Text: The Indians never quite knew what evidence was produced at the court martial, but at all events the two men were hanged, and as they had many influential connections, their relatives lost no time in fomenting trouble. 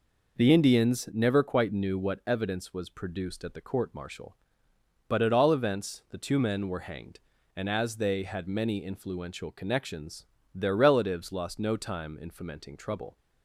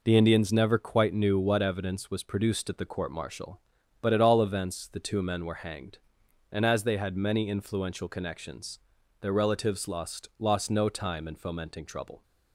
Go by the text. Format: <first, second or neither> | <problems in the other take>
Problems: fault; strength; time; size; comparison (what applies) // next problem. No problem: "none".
first | says "lost" twice; at 10.3 s